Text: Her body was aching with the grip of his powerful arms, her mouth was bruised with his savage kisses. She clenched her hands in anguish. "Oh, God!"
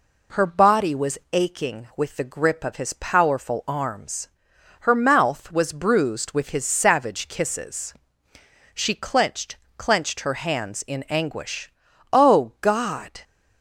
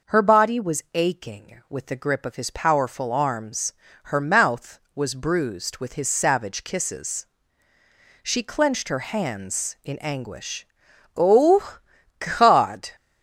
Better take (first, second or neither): second